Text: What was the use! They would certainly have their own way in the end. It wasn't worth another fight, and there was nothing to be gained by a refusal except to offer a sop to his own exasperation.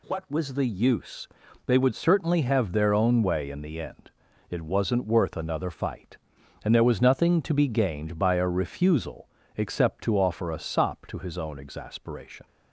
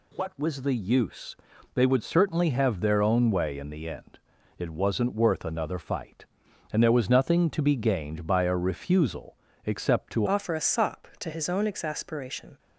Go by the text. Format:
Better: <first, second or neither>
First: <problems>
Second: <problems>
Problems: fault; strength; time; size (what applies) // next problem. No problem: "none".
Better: first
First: pauses between "refusal" and "except"; slight; at 9.2 s; 0.27 s long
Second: pauses between "refusal" and "except"; slight; at 9.3 s; 0.28 s long // changes voice at "offer"; from 10.2 s on; 2.3 s long